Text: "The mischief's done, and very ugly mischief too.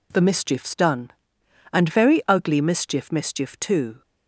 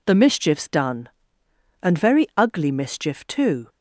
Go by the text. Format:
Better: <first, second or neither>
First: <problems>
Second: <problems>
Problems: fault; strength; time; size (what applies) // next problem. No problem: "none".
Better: second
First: says "mischief" twice; at 3.1 s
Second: none